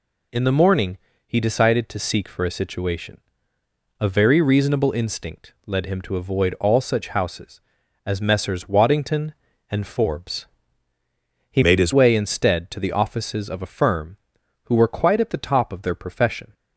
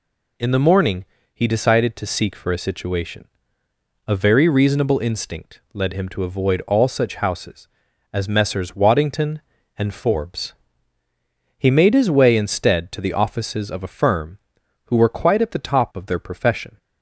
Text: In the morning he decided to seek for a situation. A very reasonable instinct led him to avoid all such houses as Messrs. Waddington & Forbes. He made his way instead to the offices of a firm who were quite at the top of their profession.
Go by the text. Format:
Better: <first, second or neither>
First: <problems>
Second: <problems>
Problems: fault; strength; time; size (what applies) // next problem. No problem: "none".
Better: second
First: pauses between "morning" and "he"; slight; at 0.9 s; 0.26 s long // changes voice from "made" to "his"; from 11.6 to 11.9 s; 0.3 s long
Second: pauses between "morning" and "he"; slight; at 1.0 s; 0.26 s long